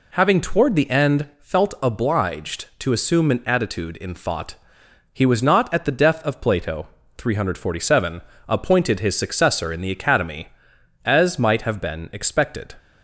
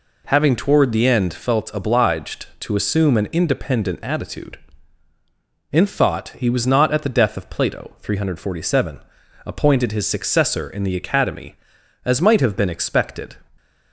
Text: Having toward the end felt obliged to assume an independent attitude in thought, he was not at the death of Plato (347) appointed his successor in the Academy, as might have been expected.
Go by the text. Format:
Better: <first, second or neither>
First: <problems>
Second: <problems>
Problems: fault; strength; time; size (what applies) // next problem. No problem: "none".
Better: second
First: skips "independent"; at 3.4 s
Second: none